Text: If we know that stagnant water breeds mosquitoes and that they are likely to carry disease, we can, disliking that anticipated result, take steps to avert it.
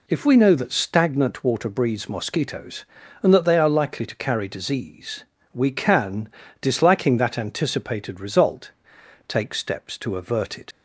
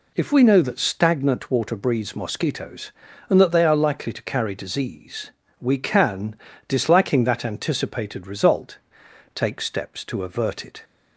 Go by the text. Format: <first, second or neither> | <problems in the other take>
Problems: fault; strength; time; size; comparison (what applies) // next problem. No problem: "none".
second | leaves "it" unfinished; at 10.7 s; 65 ms